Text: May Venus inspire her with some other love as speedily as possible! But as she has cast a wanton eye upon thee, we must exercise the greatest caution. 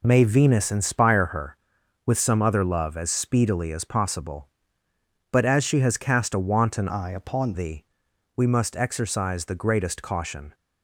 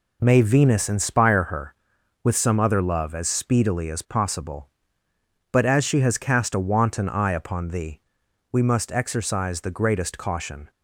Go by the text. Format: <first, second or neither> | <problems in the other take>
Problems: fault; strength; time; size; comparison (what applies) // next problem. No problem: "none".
second | changes voice from "eye" to "upon"; from 6.8 to 7.5 s; 0.7 s long